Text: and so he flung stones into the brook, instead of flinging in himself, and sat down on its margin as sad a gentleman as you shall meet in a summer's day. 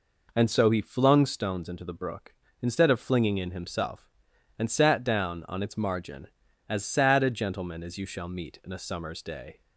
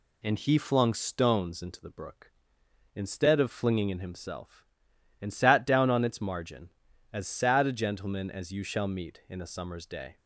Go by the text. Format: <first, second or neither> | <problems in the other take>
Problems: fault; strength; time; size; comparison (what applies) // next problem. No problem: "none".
first | skips "so"; at 0.3 s